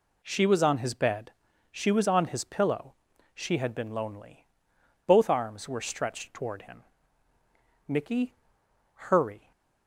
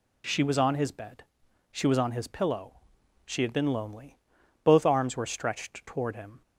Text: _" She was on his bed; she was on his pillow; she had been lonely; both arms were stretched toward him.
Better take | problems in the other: second | goes on to say "Mickey hurry"; from 7.8 s on; 1.6 s long

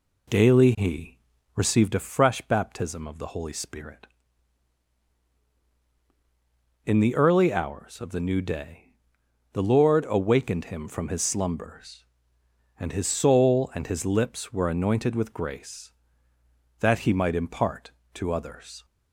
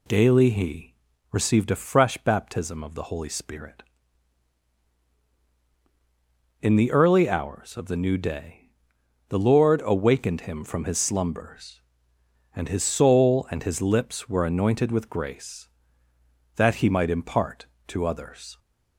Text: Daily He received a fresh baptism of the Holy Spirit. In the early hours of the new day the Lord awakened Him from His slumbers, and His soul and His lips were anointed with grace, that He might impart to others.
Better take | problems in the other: second | starts louder than the rest; slight; until 2.0 s; 3 dB // pauses between "He" and "received"; at 1.1 s; 0.38 s long; also in the second // pauses between "day" and "the"; noticeable; at 8.9 s; 0.60 s long; noticeable in the second

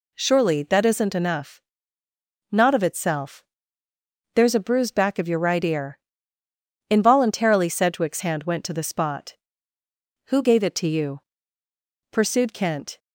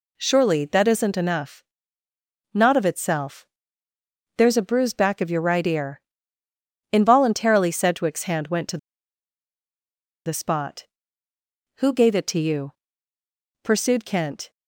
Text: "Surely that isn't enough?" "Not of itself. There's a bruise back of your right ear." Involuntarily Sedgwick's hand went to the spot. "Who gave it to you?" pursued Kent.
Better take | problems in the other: first | pauses between "to" and "the"; strong; at 8.7 s; 1.4 s long

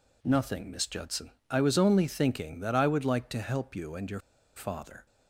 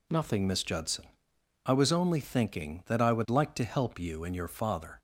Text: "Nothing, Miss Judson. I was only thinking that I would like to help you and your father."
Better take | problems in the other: second | pauses between "your" and "father"; slight; at 4.2 s; 0.35 s long

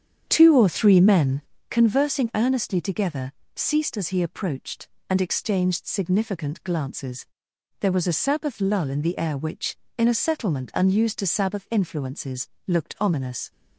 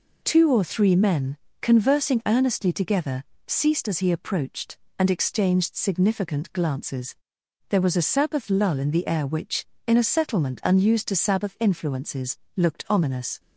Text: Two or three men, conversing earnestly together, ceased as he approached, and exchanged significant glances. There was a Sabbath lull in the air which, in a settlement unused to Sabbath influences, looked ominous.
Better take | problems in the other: second | starts louder than the rest; strong; until 1.7 s; 8.5 dB

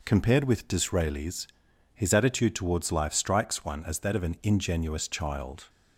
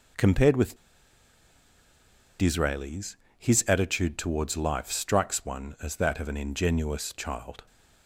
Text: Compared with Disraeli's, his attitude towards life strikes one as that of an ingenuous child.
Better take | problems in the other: first | pauses between "with" and "Disraeli's"; strong; at 0.7 s; 1.6 s long

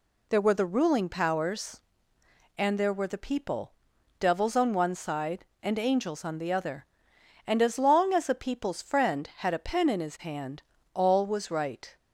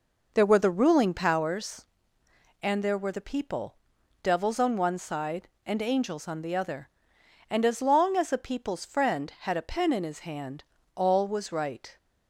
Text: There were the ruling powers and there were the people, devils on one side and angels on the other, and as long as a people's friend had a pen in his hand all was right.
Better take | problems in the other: first | starts louder than the rest; noticeable; until 1.5 s; 5 dB // pauses between "hand" and "all"; slight; at 10.6 s; 0.32 s long; slight in the first

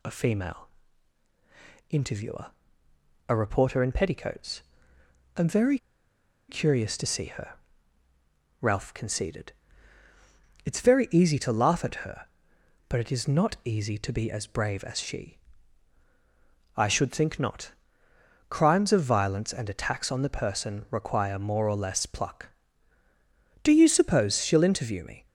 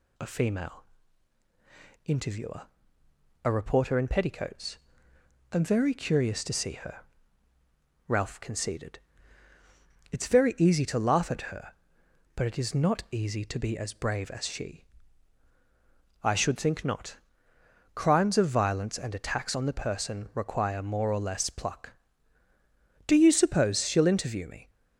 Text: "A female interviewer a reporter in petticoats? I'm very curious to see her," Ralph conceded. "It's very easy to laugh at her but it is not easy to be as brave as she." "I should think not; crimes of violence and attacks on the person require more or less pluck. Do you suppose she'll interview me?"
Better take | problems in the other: second | pauses between "female" and "interviewer"; at 0.6 s; 1.2 s long; also in the second // pauses between "interviewer" and "a"; noticeable; at 2.4 s; 0.82 s long; noticeable in the second // pauses between "very" and "curious"; noticeable; at 5.7 s; 0.72 s long

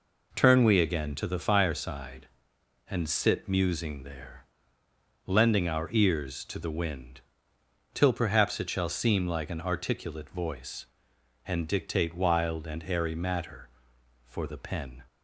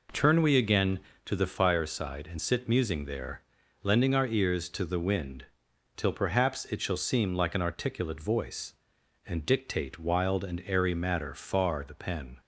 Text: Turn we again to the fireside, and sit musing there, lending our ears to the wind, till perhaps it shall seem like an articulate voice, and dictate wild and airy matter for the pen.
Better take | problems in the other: first | says "far" for "for"; at 11.3 s

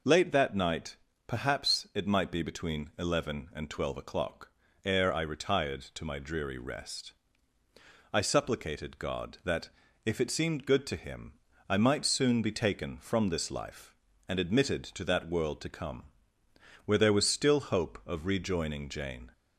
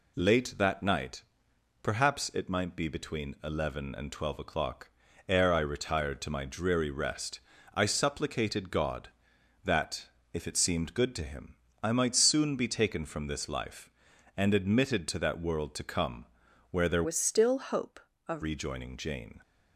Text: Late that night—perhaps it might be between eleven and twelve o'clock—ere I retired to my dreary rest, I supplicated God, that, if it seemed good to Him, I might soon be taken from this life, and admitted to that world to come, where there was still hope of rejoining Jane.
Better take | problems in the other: first | changes voice from "was" to "of"; from 17.0 to 18.4 s; 1.4 s long

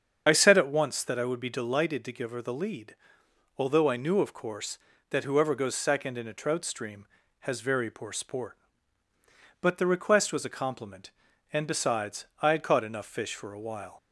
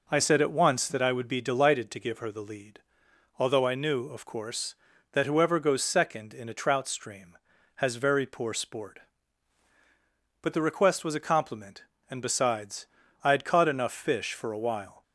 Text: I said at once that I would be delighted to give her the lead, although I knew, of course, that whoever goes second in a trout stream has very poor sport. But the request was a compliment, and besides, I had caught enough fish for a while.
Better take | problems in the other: second | loses the start of "I"; at 0.2 s; 35 ms // starts louder than the rest; strong; until 1.2 s; 7.5 dB

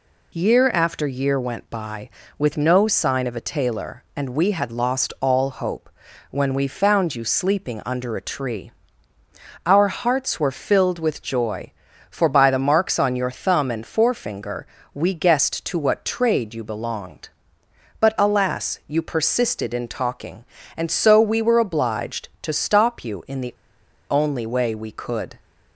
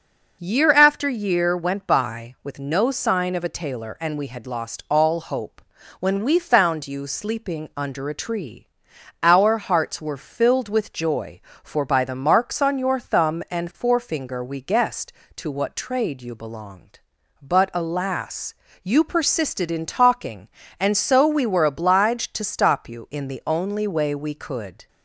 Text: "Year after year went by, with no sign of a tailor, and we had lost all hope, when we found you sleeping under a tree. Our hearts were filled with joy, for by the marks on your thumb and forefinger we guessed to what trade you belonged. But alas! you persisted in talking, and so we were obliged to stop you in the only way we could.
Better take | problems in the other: second | pauses between "forefinger" and "we"; slight; at 14.6 s; 0.28 s long // pauses between "the" and "only"; noticeable; at 23.5 s; 0.58 s long

